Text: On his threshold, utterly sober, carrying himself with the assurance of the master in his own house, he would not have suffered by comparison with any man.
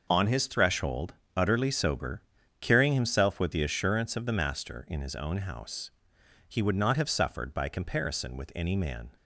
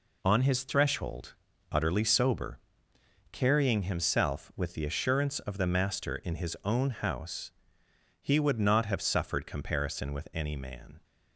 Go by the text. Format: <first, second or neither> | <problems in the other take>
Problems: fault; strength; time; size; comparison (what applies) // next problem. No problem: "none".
first | skips "by"; at 9.4 s